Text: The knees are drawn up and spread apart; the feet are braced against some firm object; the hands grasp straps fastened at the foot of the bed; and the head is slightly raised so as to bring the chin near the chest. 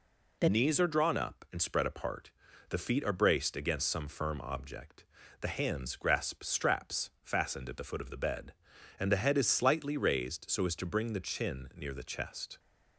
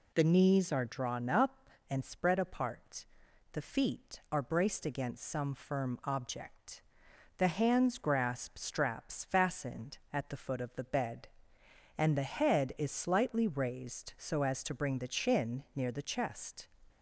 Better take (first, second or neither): second